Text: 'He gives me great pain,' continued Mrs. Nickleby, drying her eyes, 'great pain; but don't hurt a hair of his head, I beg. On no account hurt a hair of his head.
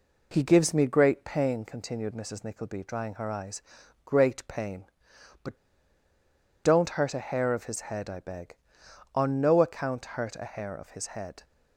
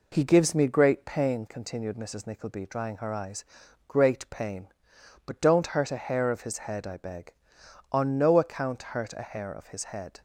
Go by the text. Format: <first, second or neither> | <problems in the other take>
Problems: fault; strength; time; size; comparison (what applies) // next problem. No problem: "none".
second | pauses between "but" and "don't"; at 5.5 s; 1.0 s long